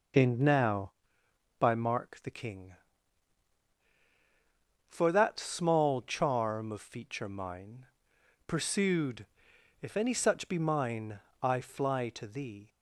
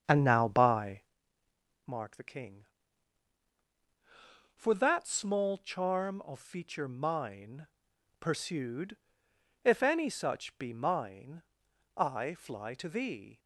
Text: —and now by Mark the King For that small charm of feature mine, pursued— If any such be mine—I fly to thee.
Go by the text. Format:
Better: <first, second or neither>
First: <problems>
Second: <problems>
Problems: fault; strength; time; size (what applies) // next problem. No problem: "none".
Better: first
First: none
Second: starts louder than the rest; strong; until 1.1 s; 8 dB // pauses between "by" and "Mark"; noticeable; at 0.9 s; 0.88 s long